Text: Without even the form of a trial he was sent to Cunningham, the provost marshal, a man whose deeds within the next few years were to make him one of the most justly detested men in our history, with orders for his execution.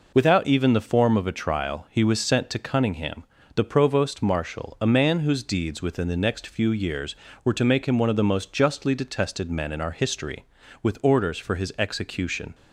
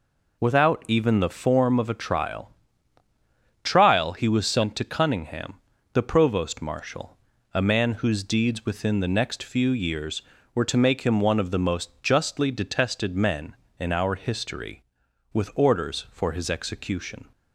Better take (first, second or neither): first